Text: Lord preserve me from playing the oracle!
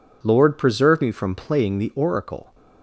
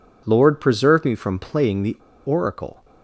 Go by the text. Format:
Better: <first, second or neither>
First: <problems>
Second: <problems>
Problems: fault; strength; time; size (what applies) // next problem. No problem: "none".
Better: first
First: none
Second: pauses between "the" and "oracle"; slight; at 1.9 s; 0.29 s long